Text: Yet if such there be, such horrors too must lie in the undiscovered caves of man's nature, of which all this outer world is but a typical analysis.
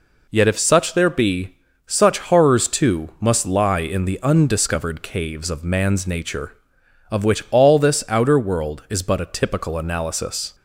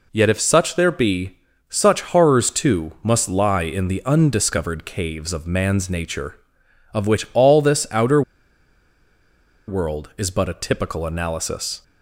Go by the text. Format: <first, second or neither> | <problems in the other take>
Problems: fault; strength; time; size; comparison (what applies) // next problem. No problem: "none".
first | pauses between "outer" and "world"; strong; at 8.2 s; 1.4 s long